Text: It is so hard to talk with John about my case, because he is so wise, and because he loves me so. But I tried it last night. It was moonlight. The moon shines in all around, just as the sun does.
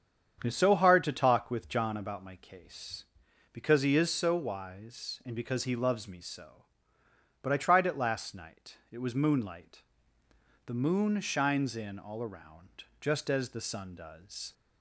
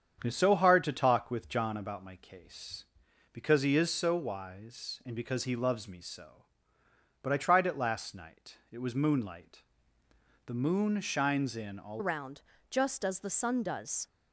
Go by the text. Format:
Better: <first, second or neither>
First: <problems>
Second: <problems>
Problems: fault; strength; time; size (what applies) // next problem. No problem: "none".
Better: first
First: starts louder than the rest; strong; until 1.4 s; 8 dB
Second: starts louder than the rest; strong; until 1.2 s; 8 dB // changes voice at "around"; from 11.9 s on; 2.1 s long